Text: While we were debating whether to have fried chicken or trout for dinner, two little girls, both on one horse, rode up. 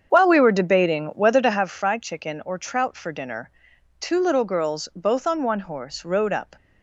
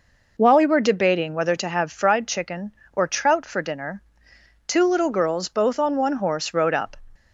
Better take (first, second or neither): second